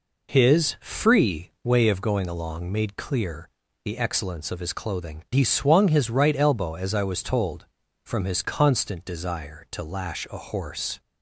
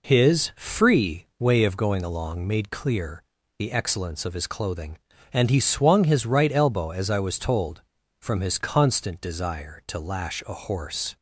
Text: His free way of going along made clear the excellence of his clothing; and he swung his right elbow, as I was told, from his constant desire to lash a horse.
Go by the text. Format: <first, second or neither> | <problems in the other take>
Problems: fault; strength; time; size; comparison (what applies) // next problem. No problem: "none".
second | pauses between "clear" and "the"; slight; at 3.4 s; 0.34 s long; slight in the second // skips "and"; at 5.2 s